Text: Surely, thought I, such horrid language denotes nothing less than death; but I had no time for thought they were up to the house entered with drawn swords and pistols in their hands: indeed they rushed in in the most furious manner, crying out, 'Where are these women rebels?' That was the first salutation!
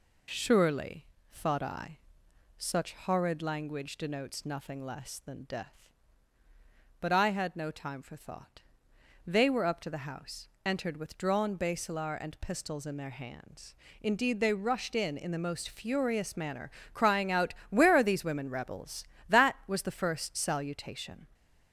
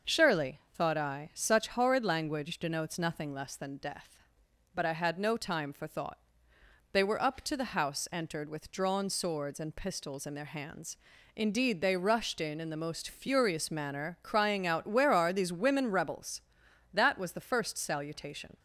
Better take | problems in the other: second | pauses between "thought" and "they"; noticeable; at 8.6 s; 0.64 s long; noticeable in the second // pauses between "house" and "entered"; slight; at 10.4 s; 0.20 s long // says "basilar" for "swords"; at 11.5 s

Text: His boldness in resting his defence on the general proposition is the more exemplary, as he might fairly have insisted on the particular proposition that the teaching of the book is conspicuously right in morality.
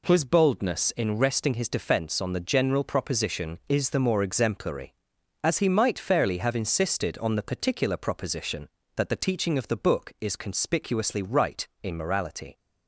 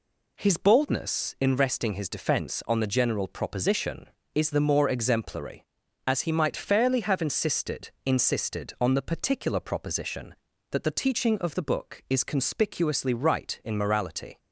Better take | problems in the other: first | says "insisted" twice; at 8.0 s

